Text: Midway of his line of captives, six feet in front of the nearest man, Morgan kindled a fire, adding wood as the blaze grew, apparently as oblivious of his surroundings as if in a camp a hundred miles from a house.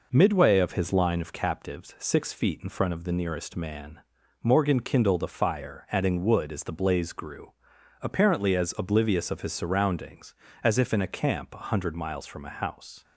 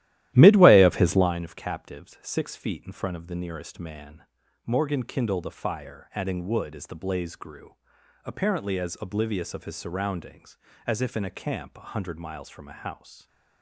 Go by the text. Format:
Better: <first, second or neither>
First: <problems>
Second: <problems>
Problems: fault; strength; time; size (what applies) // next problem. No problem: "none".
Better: first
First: none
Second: starts louder than the rest; strong; until 1.4 s; 14 dB